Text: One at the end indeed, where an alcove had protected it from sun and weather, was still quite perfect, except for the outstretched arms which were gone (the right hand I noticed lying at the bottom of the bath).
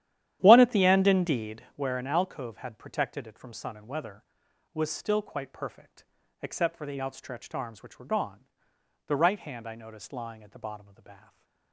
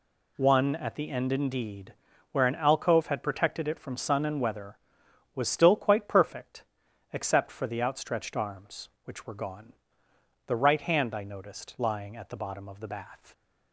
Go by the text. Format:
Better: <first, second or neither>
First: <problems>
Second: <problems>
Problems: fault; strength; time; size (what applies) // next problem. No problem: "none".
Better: second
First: starts louder than the rest; strong; until 1.8 s; 11.5 dB // stays silent after the last word; slight; from 11.1 s on; 0.6 s long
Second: none